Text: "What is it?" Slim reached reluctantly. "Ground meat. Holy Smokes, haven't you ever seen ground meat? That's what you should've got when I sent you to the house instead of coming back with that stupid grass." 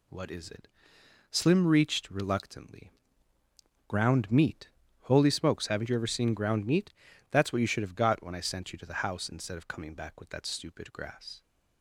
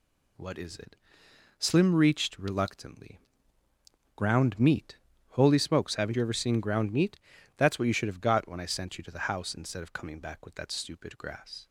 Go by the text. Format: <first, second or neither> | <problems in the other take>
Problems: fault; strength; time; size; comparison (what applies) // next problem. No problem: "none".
neither | none